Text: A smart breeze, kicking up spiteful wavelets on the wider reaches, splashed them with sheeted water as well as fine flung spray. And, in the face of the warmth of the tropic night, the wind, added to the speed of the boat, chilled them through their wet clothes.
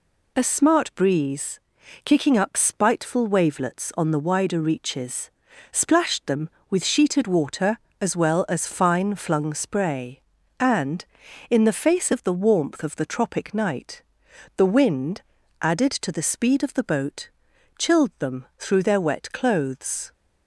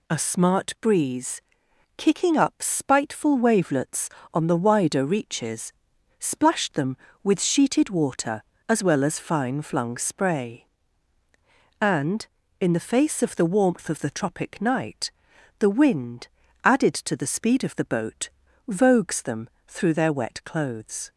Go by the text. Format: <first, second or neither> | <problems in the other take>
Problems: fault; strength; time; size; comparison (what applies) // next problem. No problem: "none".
first | says "vogues" for "chilled"; at 18.6 s // pauses between "them" and "through"; slight; at 19.4 s; 0.16 s long